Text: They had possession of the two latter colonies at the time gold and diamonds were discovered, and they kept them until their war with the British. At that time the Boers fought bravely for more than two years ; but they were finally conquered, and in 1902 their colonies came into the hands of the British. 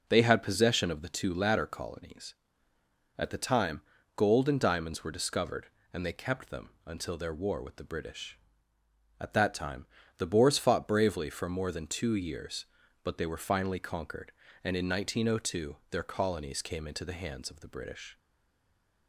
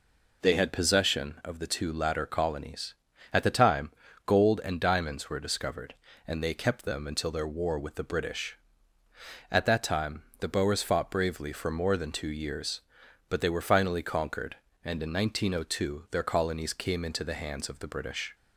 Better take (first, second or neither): second